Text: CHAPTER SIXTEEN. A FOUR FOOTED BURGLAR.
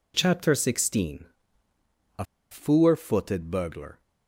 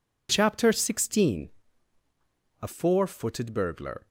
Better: second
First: pauses between "A" and "FOUR"; slight; at 2.2 s; 0.27 s long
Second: none

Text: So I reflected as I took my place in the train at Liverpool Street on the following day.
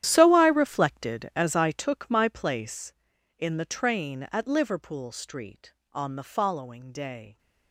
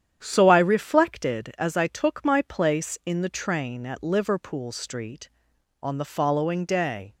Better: second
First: gets quieter; strong; throughout; 14.5 dB // starts louder than the rest; strong; until 1.0 s; 11.5 dB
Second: starts louder than the rest; strong; until 1.2 s; 9.5 dB

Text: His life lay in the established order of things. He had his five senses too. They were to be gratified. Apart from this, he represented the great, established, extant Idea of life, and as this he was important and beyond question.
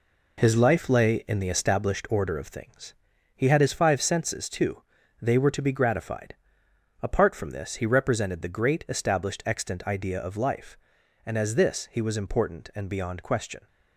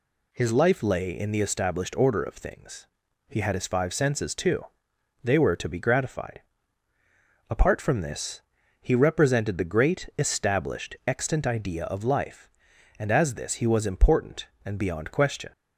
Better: second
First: gets quieter; throughout; 6.5 dB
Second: none

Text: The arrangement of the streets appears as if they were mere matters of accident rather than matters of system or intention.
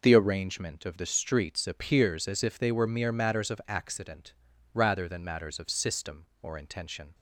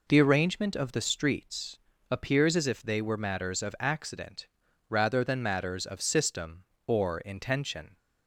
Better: first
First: pauses between "accident" and "rather"; at 4.3 s; 0.40 s long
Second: pauses between "streets" and "appears"; slight; at 1.7 s; 0.30 s long // skips "mere"; at 3.1 s // pauses between "accident" and "rather"; at 4.4 s; 0.42 s long

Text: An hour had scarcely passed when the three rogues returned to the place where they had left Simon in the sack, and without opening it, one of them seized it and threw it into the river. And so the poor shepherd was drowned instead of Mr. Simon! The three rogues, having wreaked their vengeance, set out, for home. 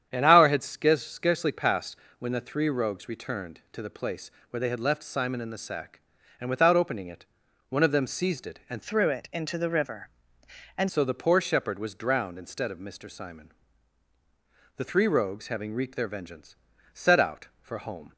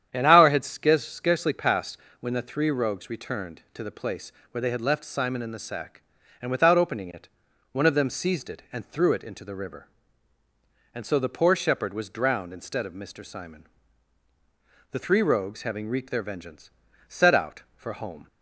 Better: second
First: starts louder than the rest; strong; until 1.1 s; 9 dB // pauses between "passed" and "when"; slight; at 1.9 s; 0.22 s long // pauses between "place" and "where"; slight; at 4.2 s; 0.20 s long // changes voice from "threw" to "And"; from 8.8 to 10.8 s; 2.0 s long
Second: starts louder than the rest; strong; until 1.1 s; 9 dB // pauses between "passed" and "when"; slight; at 1.9 s; 0.22 s long // pauses between "place" and "where"; slight; at 4.3 s; 0.20 s long

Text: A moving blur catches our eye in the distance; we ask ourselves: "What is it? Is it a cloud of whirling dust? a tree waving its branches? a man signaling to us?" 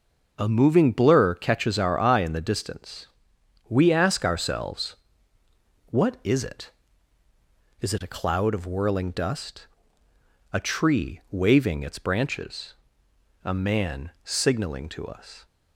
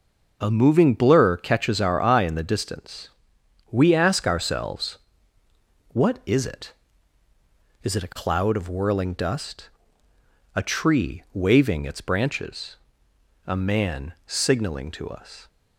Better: neither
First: none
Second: none

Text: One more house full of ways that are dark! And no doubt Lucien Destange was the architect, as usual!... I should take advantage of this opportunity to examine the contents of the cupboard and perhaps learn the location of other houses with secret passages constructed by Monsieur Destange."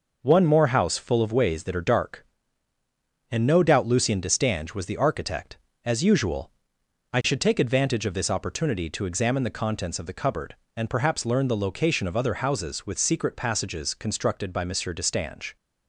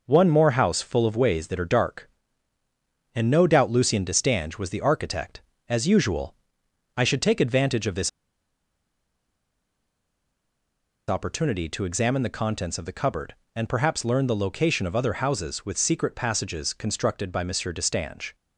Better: first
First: none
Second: pauses between "this" and "opportunity"; strong; at 8.0 s; 2.9 s long

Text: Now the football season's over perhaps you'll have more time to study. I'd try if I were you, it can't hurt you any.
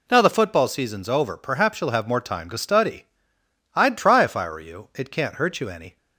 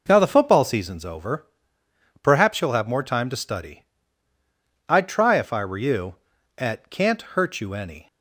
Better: first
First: none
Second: pauses between "over" and "perhaps"; noticeable; at 1.4 s; 0.76 s long // says "at" for "it"; at 6.5 s

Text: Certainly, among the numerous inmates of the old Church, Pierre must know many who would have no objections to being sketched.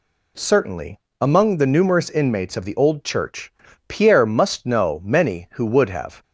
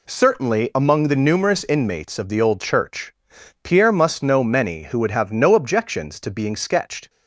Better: second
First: stops before "no objections to being sketched"; at 6.2 s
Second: none

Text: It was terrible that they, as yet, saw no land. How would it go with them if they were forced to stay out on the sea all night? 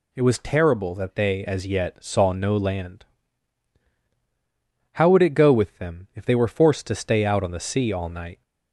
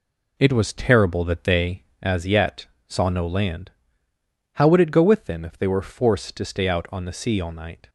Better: first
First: none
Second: starts louder than the rest; slight; until 2.2 s; 2.5 dB

